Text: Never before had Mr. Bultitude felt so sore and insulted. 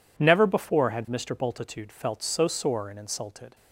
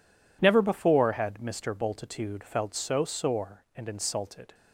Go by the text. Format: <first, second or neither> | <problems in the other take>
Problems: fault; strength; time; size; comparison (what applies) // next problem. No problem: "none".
neither | none